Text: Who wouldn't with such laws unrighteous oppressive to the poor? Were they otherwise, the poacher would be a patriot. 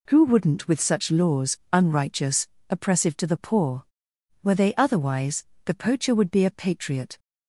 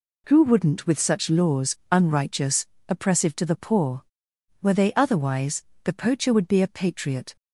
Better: neither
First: pauses between "unrighteous" and "oppressive"; slight; at 2.4 s; 0.22 s long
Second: pauses between "unrighteous" and "oppressive"; slight; at 2.6 s; 0.22 s long

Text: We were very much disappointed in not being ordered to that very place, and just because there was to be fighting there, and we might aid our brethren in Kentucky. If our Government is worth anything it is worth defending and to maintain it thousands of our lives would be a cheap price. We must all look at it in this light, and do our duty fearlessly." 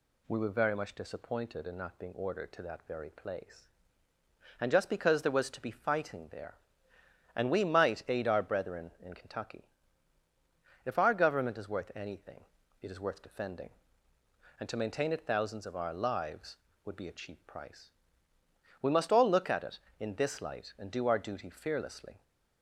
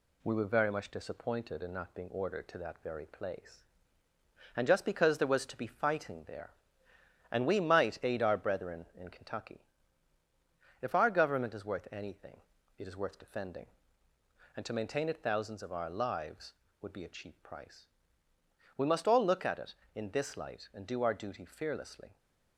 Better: first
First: pauses between "anything" and "it"; at 12.4 s; 0.40 s long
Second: gets quieter; slight; throughout; 2 dB // pauses between "anything" and "it"; at 12.3 s; 0.40 s long

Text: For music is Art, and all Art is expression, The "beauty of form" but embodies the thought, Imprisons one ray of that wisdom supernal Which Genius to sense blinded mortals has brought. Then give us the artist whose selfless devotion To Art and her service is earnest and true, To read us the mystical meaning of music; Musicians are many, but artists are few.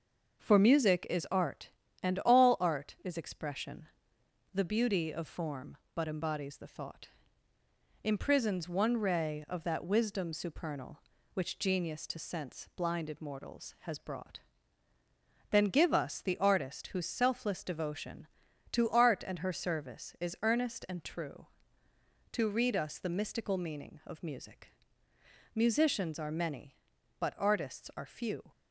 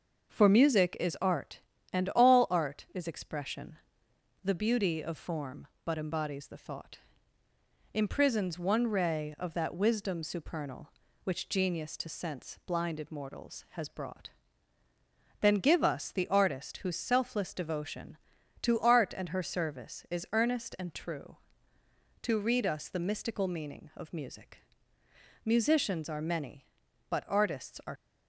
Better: first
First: starts louder than the rest; noticeable; until 1.4 s; 6 dB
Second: starts louder than the rest; noticeable; until 1.3 s; 6 dB // stops before "few"; at 27.9 s

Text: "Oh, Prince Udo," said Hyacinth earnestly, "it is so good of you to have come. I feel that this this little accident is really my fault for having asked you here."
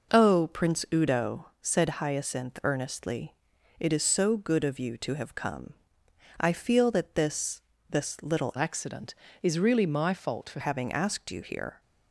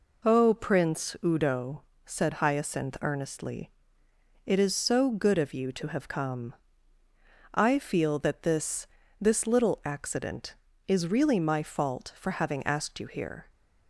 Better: second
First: pauses between "this" and "this"; slight; at 7.5 s; 0.30 s long // changes voice from "accident" to "for"; from 8.5 to 10.5 s; 2.0 s long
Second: pauses between "this" and "this"; slight; at 8.8 s; 0.32 s long

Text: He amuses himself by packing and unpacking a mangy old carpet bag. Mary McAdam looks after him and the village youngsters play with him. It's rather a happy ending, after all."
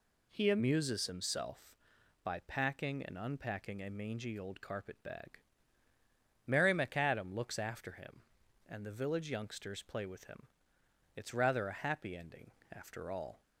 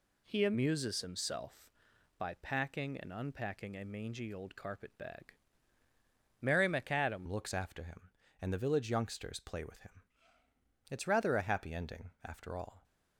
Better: first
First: none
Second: changes voice at "looks"; from 7.2 s on; 5.6 s long

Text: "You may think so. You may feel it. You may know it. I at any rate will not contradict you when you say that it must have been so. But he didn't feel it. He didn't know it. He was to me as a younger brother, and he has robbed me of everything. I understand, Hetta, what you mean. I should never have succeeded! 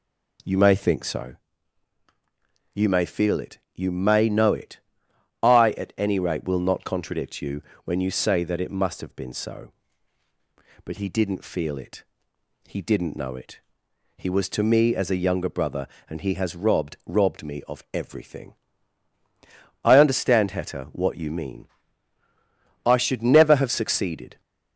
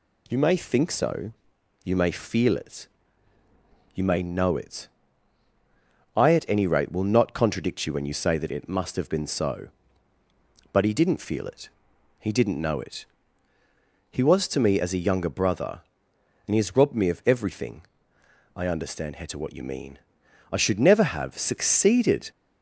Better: second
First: pauses between "you" and "when"; slight; at 7.6 s; 0.24 s long // says "robbed" twice; at 17.0 s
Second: none

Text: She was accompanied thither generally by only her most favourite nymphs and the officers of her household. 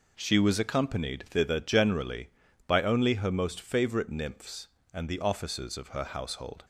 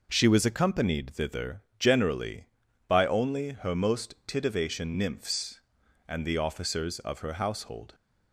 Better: first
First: none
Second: pauses between "thither" and "generally"; slight; at 1.6 s; 0.16 s long // says "titivation" for "favourite"; at 4.2 s

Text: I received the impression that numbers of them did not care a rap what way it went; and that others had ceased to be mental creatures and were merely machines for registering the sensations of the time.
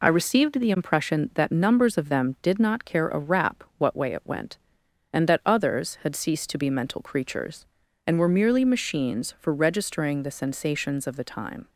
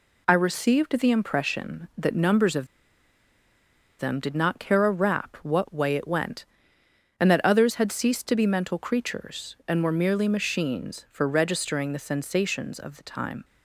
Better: first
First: none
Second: pauses between "of" and "them"; strong; at 2.6 s; 1.3 s long

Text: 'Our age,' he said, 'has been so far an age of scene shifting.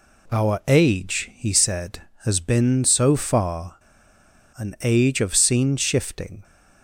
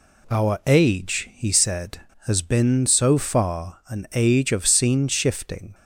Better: second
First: pauses between "far" and "an"; noticeable; at 3.7 s; 0.80 s long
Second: none

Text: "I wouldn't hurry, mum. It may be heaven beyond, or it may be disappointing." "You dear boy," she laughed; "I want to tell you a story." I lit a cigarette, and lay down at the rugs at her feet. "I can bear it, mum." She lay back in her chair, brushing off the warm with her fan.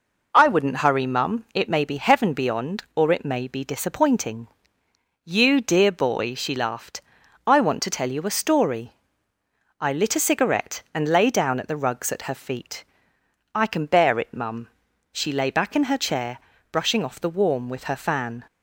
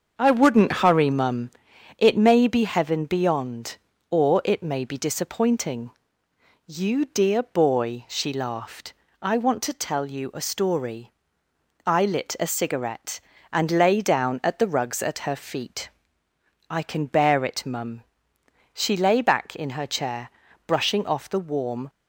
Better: first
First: none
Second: starts louder than the rest; until 1.2 s; 6.5 dB // stops before "with her fan"; at 21.8 s

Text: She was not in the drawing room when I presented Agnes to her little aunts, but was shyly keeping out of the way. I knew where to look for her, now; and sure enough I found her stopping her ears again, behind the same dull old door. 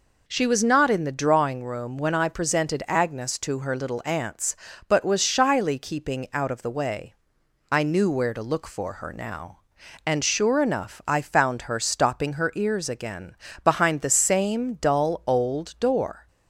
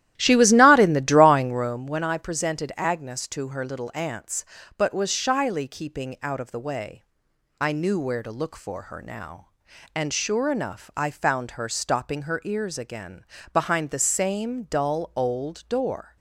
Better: first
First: none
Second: starts louder than the rest; strong; until 1.9 s; 13 dB

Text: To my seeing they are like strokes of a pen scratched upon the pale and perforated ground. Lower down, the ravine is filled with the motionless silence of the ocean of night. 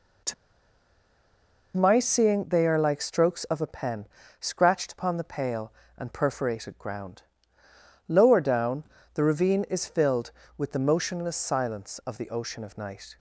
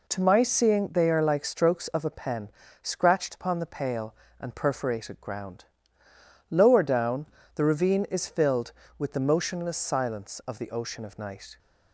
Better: second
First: pauses between "To" and "my"; strong; at 0.3 s; 1.4 s long // pauses between "pen" and "scratched"; slight; at 4.0 s; 0.32 s long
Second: pauses between "pen" and "scratched"; slight; at 2.5 s; 0.30 s long

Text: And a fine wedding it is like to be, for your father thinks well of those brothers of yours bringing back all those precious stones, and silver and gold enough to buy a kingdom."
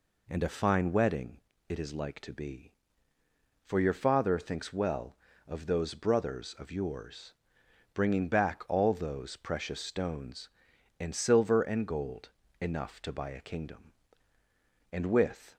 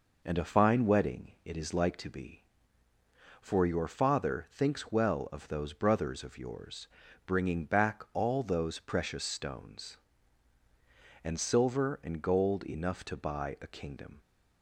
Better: second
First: pauses between "wedding" and "it"; slight; at 1.3 s; 0.30 s long // pauses between "yours" and "bringing"; noticeable; at 7.3 s; 0.62 s long // pauses between "gold" and "enough"; slight; at 12.2 s; 0.32 s long // goes on to say "And with"; noticeable; from 14.9 s on; 0.64 s long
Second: pauses between "yours" and "bringing"; slight; at 6.8 s; 0.36 s long

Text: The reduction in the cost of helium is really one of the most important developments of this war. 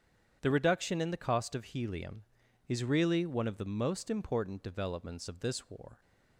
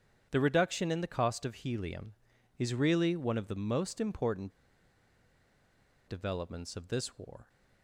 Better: first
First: starts louder than the rest; strong; until 1.4 s; 8.5 dB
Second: starts louder than the rest; strong; until 1.3 s; 8.5 dB // pauses between "important" and "developments"; strong; at 4.5 s; 1.5 s long

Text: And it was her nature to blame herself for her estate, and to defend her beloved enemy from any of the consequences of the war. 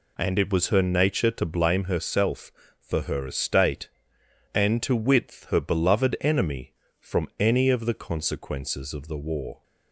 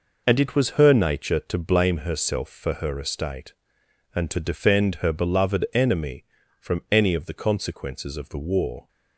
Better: second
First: says "width" for "defend"; at 4.9 s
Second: none

